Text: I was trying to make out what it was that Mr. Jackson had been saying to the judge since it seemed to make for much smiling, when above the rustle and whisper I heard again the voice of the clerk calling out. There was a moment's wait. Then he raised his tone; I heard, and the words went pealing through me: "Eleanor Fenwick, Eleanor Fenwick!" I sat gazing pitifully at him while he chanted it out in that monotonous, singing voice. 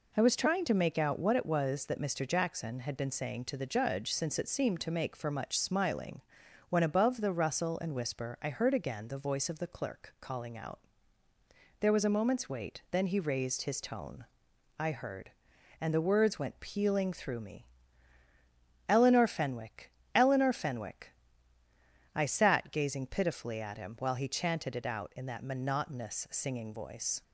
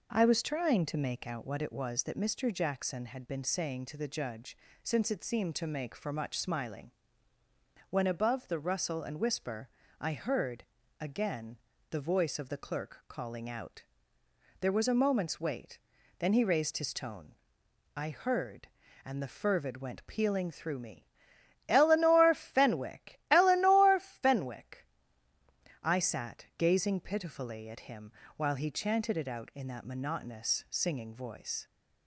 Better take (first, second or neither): first